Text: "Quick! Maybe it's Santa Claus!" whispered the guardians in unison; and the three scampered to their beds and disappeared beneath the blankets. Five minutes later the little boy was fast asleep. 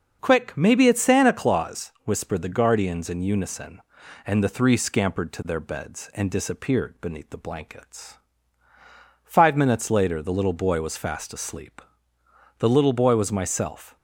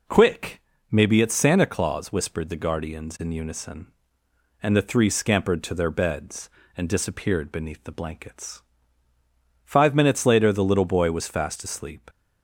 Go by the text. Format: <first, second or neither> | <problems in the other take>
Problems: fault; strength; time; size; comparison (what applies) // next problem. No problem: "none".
second | starts louder than the rest; until 1.2 s; 6.5 dB // goes on to say "The little boy was myself"; from 12.5 s on; 1.3 s long